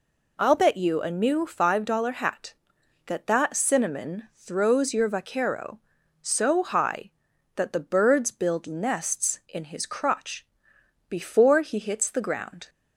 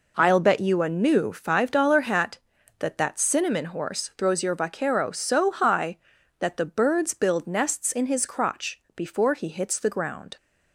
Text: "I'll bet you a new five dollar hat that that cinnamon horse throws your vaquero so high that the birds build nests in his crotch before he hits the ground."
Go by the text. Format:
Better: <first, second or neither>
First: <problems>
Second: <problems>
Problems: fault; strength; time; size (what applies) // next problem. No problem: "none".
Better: second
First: skips "horse"; at 4.3 s // pauses between "crotch" and "before"; noticeable; at 10.4 s; 0.60 s long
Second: none